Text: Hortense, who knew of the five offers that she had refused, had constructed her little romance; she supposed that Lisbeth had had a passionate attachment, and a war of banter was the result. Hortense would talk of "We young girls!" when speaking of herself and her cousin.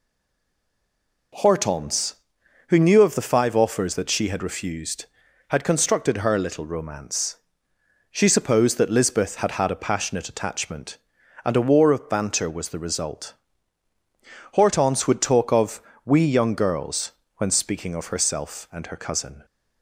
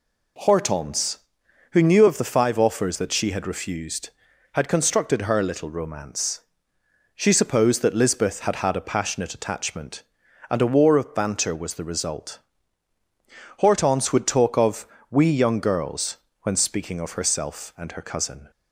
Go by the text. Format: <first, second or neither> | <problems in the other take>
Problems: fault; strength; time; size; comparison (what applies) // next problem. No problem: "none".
second | stays silent before the first word; noticeable; until 1.3 s; 1.3 s long // pauses between "of" and "We"; slight; at 15.8 s; 0.24 s long; slight in the second